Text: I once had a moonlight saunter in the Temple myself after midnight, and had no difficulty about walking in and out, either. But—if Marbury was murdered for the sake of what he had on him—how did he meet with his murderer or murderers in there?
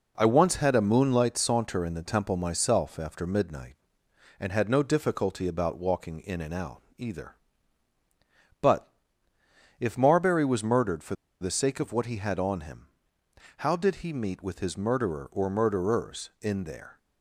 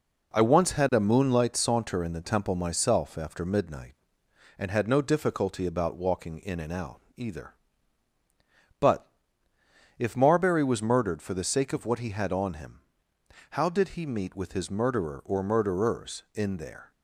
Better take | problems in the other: second | pauses between "for" and "the"; slight; at 11.1 s; 0.26 s long

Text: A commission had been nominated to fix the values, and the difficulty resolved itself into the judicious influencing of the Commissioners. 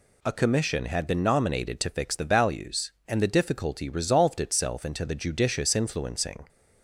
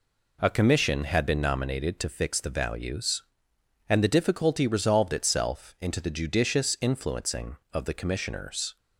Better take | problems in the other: second | stops before "of the Commissioners"; at 6.4 s

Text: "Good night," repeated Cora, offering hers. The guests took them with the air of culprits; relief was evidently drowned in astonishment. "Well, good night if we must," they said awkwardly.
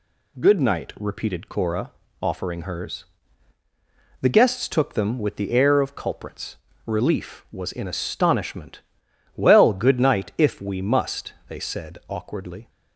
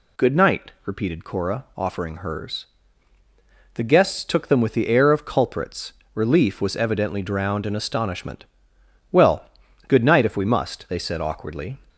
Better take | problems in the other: second | skips "evidently drowned"; at 7.7 s

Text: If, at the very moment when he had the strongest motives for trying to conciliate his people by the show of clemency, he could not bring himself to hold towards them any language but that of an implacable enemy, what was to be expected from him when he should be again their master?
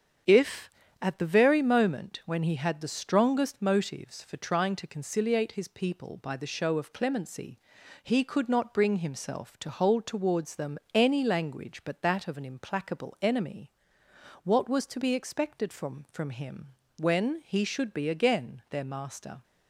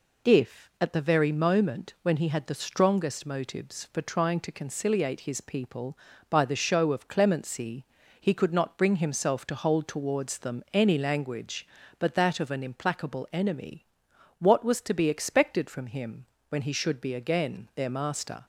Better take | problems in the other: second | starts louder than the rest; strong; until 1.5 s; 7.5 dB // pauses between "them" and "any"; slight; at 10.7 s; 0.16 s long // says "from" twice; at 16.1 s // pauses between "him" and "when"; slight; at 16.7 s; 0.26 s long; slight in the second

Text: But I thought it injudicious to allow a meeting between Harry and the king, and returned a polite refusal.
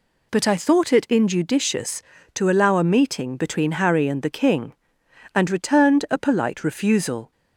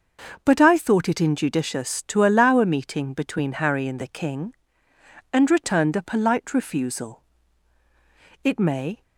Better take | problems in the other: first | starts louder than the rest; until 1.4 s; 6 dB // goes on to say "It may"; from 8.4 s on; 0.58 s long

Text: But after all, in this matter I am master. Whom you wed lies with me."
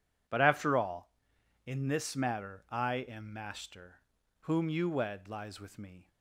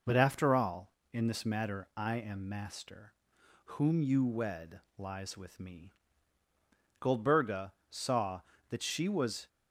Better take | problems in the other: first | pauses between "wed" and "lies"; slight; at 4.7 s; 0.18 s long // goes on to say "Goldberga saw that she was"; strong; from 7.0 s on; 2.4 s long

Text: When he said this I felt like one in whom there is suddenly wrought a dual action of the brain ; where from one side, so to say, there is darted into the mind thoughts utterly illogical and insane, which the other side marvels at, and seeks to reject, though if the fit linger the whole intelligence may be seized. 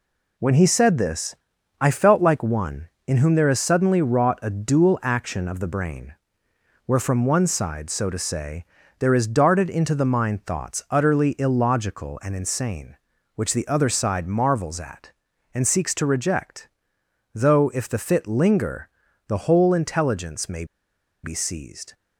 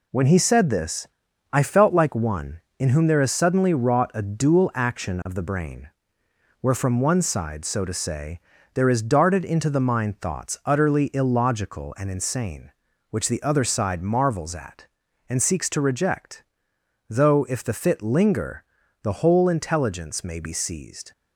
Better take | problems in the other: second | pauses between "this" and "I"; noticeable; at 1.3 s; 0.46 s long; noticeable in the second // pauses between "linger" and "the"; at 18.8 s; 0.40 s long; also in the second // pauses between "may" and "be"; noticeable; at 20.6 s; 0.58 s long

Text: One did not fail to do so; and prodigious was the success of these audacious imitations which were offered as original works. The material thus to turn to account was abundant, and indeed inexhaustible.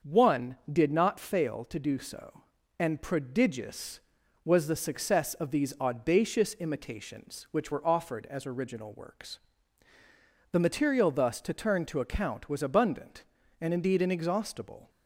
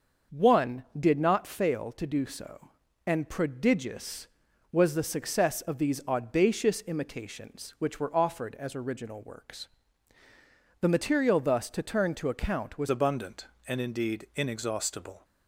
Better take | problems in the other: first | starts louder than the rest; until 1.4 s; 6.5 dB; also in the first // changes voice at "abundant"; from 12.9 s on; 2.3 s long

